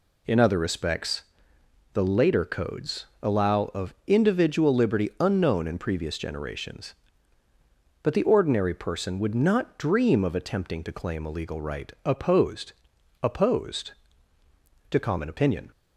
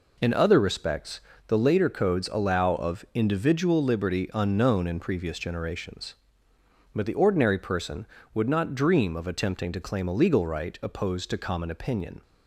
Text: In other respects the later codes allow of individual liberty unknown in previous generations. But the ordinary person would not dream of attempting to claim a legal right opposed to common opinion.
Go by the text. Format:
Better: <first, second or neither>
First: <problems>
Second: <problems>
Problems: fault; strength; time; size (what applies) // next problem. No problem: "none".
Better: second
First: pauses between "respects" and "the"; noticeable; at 1.2 s; 0.70 s long // pauses between "codes" and "allow"; slight; at 3.0 s; 0.18 s long // says "opposed" twice; at 13.2 s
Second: pauses between "respects" and "the"; slight; at 1.1 s; 0.26 s long